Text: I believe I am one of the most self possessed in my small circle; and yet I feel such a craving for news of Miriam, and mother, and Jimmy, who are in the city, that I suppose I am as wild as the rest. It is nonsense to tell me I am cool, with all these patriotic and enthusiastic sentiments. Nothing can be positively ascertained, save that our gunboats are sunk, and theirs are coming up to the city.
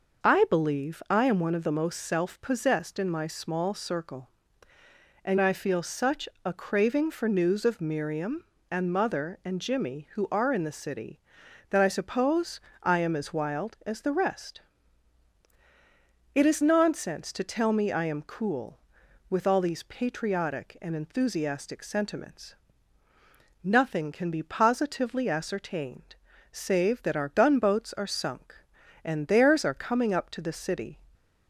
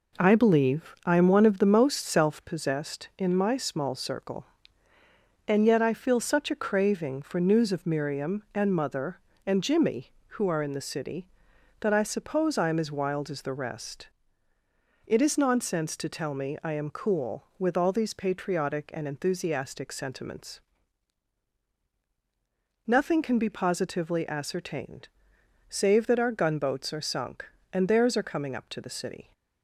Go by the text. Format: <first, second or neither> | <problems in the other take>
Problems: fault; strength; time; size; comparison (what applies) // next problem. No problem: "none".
second | starts louder than the rest; noticeable; until 1.3 s; 6 dB // skips "yet"; at 5.3 s // pauses between "such" and "a"; slight; at 6.2 s; 0.16 s long // pauses between "suppose" and "I"; slight; at 12.6 s; 0.24 s long